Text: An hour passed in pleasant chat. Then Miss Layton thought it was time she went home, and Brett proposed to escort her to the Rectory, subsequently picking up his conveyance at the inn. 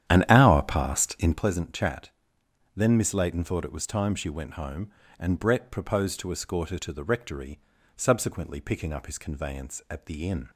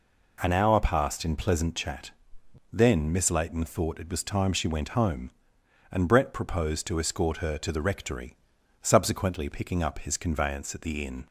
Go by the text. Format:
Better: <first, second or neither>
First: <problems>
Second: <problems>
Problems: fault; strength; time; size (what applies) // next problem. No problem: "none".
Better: second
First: starts louder than the rest; strong; until 1.5 s; 10.5 dB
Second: none